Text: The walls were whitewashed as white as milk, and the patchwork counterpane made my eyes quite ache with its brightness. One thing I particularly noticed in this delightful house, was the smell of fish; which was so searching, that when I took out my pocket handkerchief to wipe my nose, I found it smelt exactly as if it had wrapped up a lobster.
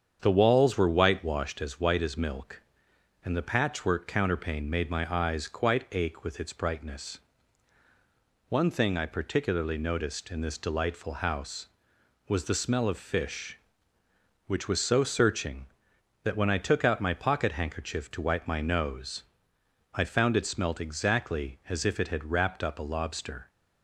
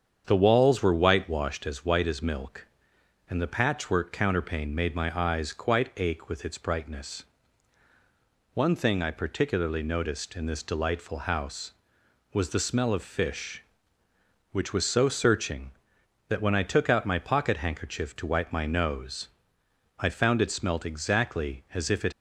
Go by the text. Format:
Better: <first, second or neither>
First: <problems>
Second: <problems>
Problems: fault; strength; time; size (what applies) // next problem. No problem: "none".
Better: first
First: starts louder than the rest; strong; until 1.2 s; 7.5 dB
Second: starts louder than the rest; strong; until 1.2 s; 7.5 dB // stops before "had wrapped up a lobster"; at 22.1 s